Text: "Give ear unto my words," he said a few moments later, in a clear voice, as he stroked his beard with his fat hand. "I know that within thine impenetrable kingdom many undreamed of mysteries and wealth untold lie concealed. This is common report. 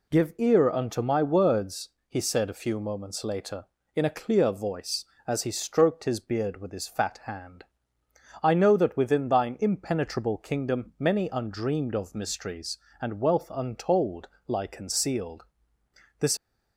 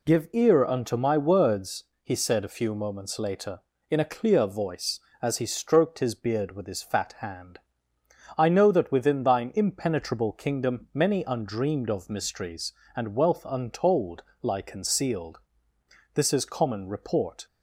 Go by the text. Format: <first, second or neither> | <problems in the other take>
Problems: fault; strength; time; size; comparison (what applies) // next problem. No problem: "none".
second | pauses between "untold" and "lie"; slight; at 14.2 s; 0.18 s long; slight in the second // stops before "is common report"; at 16.3 s